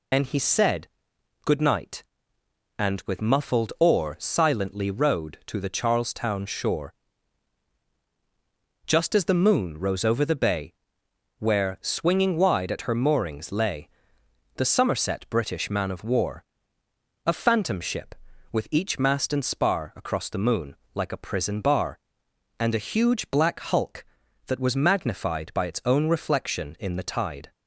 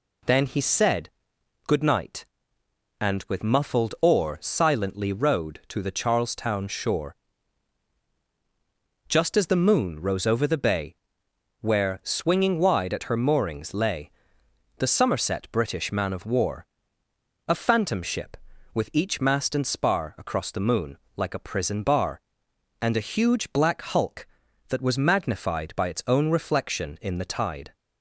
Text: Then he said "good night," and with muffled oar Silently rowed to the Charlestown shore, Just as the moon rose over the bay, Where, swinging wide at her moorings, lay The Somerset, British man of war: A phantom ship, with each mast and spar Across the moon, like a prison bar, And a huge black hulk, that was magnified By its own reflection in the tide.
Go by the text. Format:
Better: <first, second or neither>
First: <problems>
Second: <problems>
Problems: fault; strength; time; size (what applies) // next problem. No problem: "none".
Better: second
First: loses the start of "Then"; at 0.1 s; 110 ms // pauses between "said" and "good"; noticeable; at 0.8 s; 0.56 s long // pauses between "lay" and "The"; noticeable; at 13.8 s; 0.68 s long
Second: pauses between "said" and "good"; noticeable; at 1.0 s; 0.56 s long // pauses between "lay" and "The"; noticeable; at 14.0 s; 0.68 s long